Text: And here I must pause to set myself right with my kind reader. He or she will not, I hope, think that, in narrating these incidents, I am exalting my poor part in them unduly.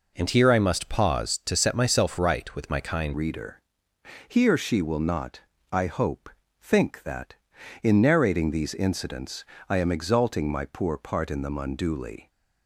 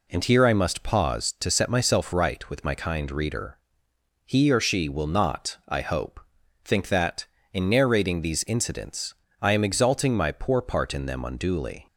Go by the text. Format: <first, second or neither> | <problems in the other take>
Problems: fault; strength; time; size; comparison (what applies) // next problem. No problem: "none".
second | changes voice at "reader"; from 3.1 s on; 9.1 s long